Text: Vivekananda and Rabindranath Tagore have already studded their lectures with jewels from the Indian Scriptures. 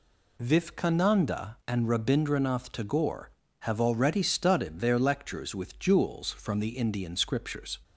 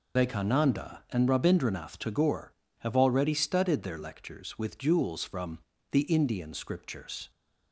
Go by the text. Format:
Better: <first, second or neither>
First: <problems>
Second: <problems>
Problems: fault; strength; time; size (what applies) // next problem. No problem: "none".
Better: first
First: none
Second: loses the start of "Vivekananda"; at 0.1 s; 145 ms // pauses between "from" and "the"; slight; at 5.6 s; 0.32 s long